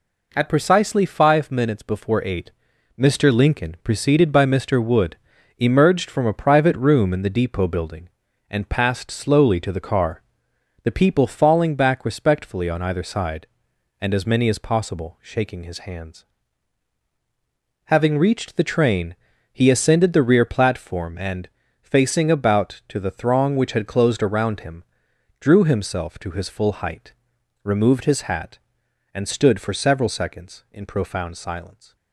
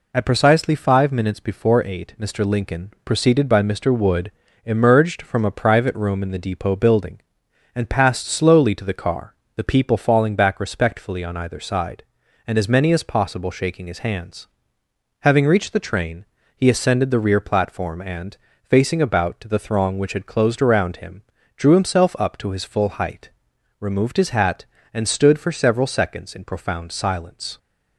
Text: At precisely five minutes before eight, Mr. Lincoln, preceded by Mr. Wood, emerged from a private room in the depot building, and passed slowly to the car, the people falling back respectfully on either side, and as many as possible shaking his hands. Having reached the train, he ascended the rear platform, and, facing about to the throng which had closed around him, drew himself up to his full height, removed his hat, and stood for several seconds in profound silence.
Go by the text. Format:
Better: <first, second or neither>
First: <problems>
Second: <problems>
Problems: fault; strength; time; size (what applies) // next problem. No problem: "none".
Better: second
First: skips "up"; at 26.1 s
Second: none